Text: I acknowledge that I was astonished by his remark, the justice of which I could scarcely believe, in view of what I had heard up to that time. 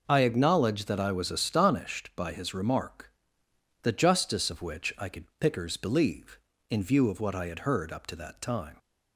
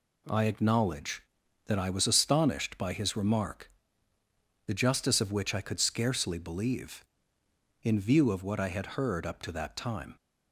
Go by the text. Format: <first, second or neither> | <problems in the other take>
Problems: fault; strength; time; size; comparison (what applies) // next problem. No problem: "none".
second | says "pickers" for "scarcely"; at 5.3 s